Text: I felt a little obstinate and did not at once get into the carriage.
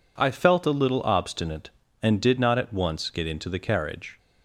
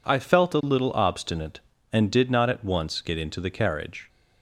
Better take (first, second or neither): neither